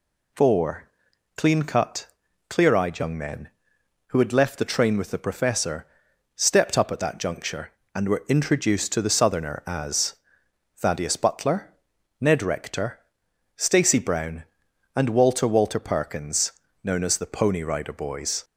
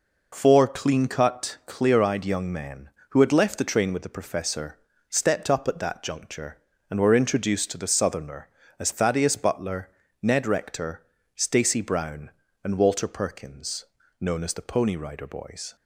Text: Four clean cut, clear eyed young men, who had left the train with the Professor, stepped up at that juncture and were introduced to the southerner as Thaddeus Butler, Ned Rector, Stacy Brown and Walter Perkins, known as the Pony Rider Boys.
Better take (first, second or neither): second